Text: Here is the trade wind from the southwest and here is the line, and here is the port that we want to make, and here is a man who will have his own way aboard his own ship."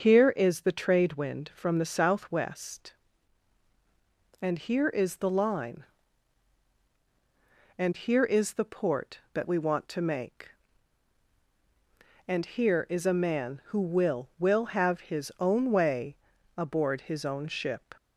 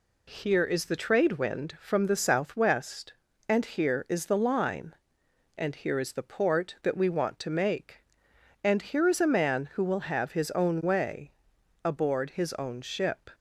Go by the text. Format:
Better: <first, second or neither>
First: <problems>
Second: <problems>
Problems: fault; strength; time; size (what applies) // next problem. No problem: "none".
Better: second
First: starts louder than the rest; until 1.0 s; 6.5 dB // says "will" twice; at 14.3 s // pauses between "way" and "aboard"; at 16.1 s; 0.42 s long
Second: pauses between "way" and "aboard"; noticeable; at 11.3 s; 0.52 s long